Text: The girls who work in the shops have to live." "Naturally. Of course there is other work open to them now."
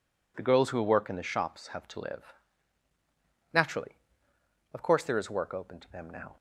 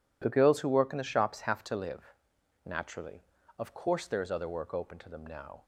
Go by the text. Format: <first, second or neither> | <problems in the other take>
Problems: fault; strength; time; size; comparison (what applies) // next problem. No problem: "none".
second | skips "other"; at 5.3 s